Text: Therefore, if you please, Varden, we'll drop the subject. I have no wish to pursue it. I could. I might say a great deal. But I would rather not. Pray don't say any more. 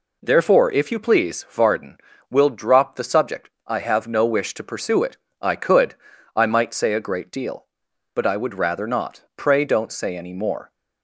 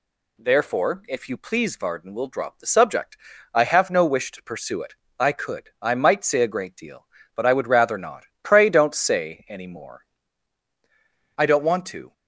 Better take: first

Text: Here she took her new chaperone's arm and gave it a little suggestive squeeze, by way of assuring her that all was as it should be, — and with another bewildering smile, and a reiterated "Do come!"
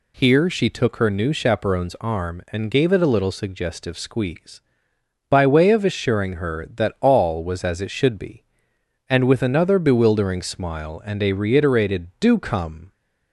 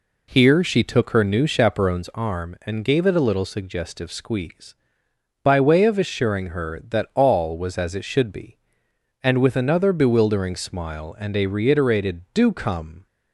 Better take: first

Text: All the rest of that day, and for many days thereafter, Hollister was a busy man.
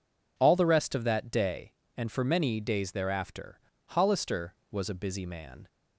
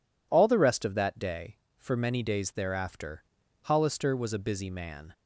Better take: first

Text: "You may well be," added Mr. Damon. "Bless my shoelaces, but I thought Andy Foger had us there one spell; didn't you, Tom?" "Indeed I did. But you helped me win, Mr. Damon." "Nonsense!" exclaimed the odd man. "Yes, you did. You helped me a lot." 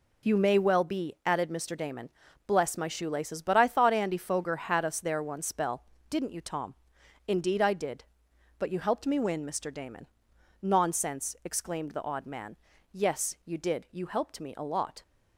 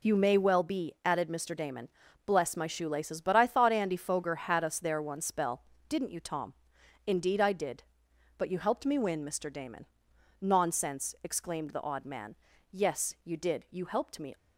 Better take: first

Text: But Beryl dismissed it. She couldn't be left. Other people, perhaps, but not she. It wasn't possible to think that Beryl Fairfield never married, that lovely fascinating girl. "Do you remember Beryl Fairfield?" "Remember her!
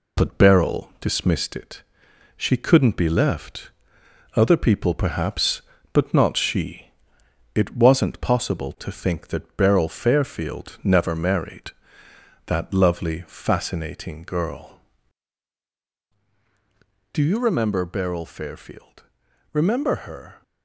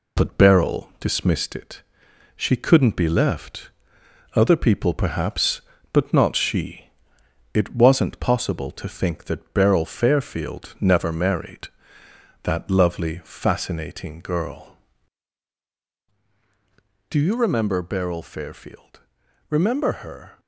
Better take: neither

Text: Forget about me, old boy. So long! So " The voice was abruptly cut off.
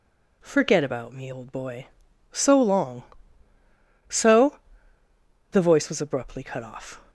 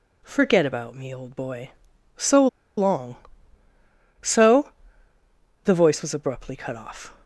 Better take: first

